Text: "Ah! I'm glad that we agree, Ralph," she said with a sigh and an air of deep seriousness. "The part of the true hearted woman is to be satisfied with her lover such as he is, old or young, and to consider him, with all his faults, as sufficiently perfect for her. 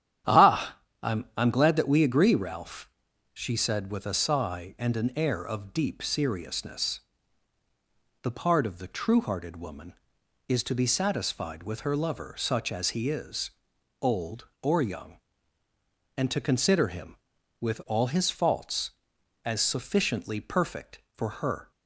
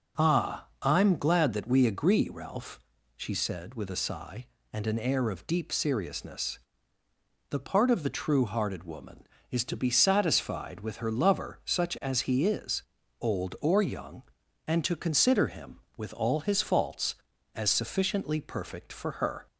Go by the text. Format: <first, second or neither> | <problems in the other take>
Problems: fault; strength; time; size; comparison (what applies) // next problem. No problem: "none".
second | starts louder than the rest; strong; until 1.6 s; 10 dB // says "I'm" twice; at 1.3 s